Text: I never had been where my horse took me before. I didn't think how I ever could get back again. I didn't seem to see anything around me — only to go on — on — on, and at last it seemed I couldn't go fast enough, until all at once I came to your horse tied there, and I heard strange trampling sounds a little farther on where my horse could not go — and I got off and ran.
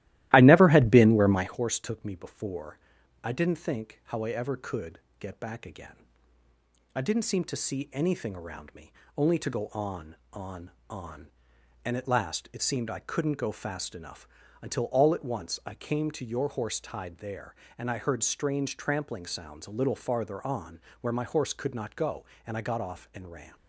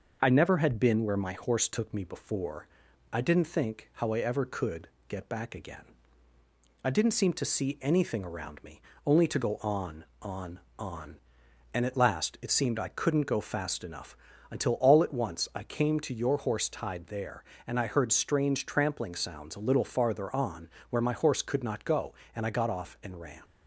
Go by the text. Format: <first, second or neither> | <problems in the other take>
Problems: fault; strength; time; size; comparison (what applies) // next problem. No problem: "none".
second | starts louder than the rest; strong; until 1.6 s; 15.5 dB // pauses between "could" and "get"; slight; at 4.9 s; 0.22 s long; slight in the second // pauses between "on" and "where"; slight; at 20.8 s; 0.22 s long; slight in the second